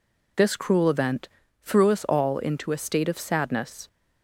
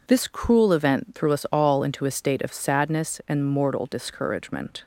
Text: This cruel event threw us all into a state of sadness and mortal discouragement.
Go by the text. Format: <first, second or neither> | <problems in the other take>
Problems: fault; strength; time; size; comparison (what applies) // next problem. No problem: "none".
second | pauses between "event" and "threw"; slight; at 1.2 s; 0.32 s long // stops before "and mortal discouragement"; at 3.8 s